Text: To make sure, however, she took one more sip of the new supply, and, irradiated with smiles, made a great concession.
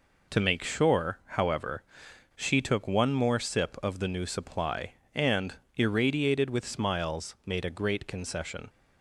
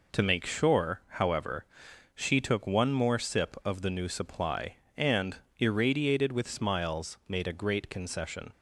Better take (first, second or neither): neither